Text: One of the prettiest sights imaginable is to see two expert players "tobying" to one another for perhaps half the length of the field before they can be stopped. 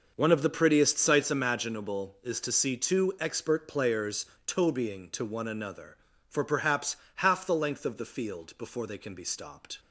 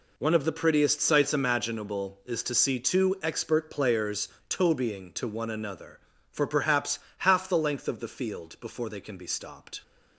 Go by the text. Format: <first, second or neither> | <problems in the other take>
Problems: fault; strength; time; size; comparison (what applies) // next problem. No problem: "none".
second | starts louder than the rest; noticeable; until 1.3 s; 6 dB // pauses between "players" and "tobying"; slight; at 4.2 s; 0.20 s long; slight in the second // pauses between "perhaps" and "half"; slight; at 6.9 s; 0.20 s long; slight in the second